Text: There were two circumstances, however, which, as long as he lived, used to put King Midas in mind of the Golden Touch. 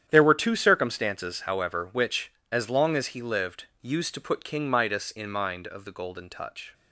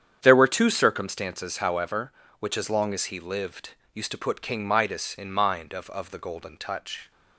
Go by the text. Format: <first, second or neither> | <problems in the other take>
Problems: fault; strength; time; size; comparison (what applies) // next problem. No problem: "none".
first | starts louder than the rest; strong; until 1.2 s; 8.5 dB; strong in the first // says "of" twice; at 5.8 s